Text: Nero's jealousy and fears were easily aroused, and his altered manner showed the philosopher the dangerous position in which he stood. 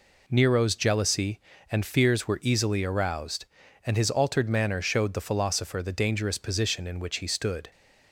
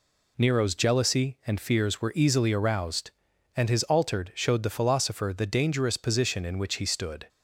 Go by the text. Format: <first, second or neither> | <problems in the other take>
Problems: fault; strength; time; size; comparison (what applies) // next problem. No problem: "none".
first | skips "manner"; at 4.3 s